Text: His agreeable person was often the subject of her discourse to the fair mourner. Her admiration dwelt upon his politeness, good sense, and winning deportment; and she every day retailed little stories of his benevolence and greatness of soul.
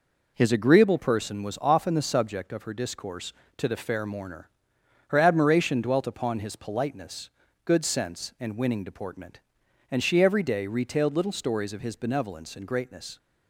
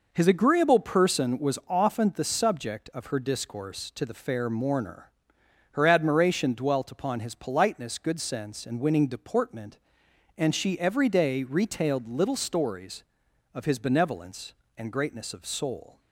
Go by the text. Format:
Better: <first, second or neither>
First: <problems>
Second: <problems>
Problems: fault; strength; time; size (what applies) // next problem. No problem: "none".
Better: second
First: stops before "of soul"; at 13.1 s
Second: none